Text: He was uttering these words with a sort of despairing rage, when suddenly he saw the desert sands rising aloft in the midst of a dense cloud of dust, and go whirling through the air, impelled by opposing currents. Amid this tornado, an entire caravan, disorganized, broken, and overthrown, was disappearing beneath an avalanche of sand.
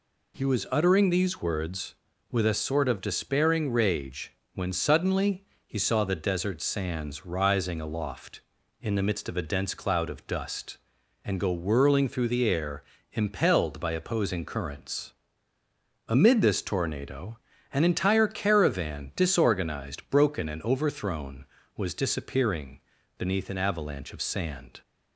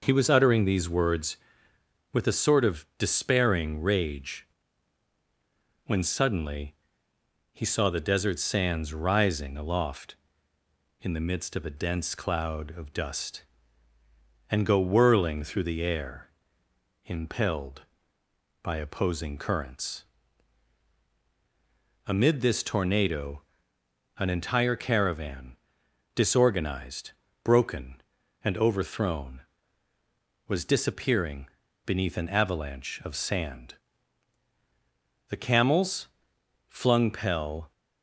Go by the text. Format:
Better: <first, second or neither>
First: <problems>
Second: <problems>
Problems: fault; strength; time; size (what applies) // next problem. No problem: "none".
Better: first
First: pauses between "suddenly" and "he"; slight; at 5.4 s; 0.20 s long // pauses between "disappearing" and "beneath"; slight; at 22.8 s; 0.36 s long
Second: pauses between "suddenly" and "he"; noticeable; at 6.7 s; 0.78 s long // pauses between "disappearing" and "beneath"; at 31.4 s; 0.38 s long // goes on to say "The camels flung pell"; strong; from 35.2 s on; 2.4 s long